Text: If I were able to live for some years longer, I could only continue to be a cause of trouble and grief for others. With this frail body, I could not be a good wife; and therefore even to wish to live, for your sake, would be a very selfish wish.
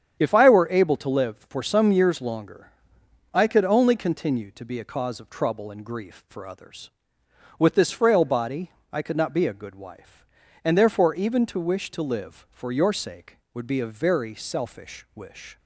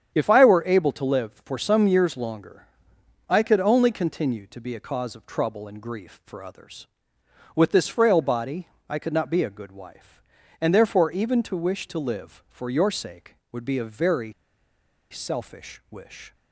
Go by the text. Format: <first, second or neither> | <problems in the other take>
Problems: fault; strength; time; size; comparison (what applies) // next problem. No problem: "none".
first | starts louder than the rest; strong; until 1.1 s; 8.5 dB; strong in the first // pauses between "very" and "selfish"; noticeable; at 14.3 s; 0.77 s long